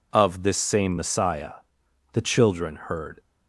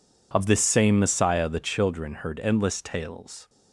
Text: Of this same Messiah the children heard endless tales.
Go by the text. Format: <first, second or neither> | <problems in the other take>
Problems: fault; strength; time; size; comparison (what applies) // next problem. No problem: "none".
second | pauses between "Messiah" and "the"; noticeable; at 1.5 s; 0.60 s long // stops before "endless tales"; at 3.1 s